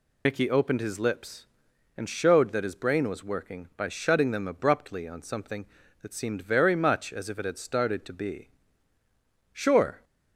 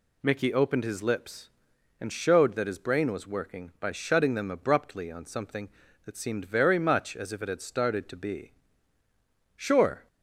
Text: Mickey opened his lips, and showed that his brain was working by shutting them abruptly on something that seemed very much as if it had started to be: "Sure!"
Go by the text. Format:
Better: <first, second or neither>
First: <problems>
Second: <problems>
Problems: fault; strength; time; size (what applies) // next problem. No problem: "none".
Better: second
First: loses the start of "Mickey"; at 0.2 s; 55 ms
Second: none